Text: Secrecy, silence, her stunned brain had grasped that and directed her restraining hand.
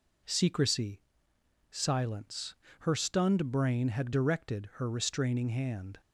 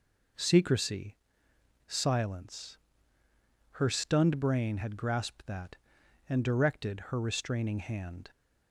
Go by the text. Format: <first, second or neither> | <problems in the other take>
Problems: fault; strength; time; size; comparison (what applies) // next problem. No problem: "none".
second | skips "grasped that and"; at 4.1 s